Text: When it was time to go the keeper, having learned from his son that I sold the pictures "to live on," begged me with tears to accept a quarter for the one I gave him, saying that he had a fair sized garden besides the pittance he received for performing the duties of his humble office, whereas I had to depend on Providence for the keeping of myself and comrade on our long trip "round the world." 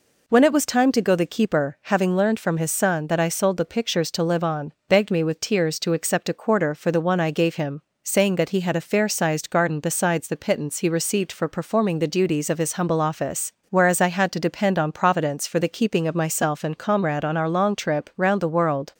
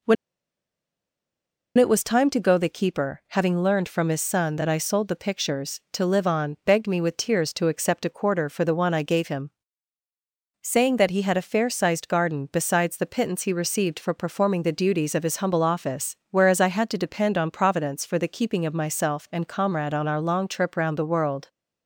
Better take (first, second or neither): first